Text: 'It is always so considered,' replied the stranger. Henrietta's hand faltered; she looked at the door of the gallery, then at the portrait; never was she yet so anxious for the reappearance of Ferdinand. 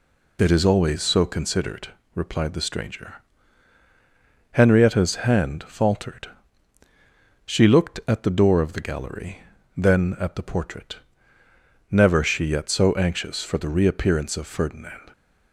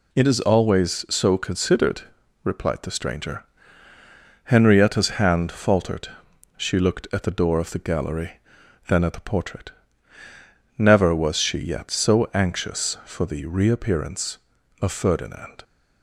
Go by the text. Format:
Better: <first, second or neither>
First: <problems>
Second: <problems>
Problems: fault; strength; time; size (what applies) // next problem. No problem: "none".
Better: second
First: skips "was"; at 12.2 s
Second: none